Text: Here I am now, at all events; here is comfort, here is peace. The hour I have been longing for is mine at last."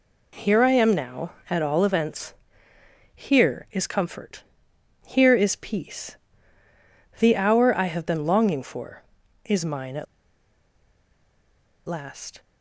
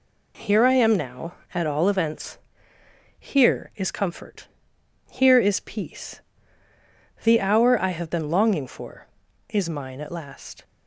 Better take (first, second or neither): second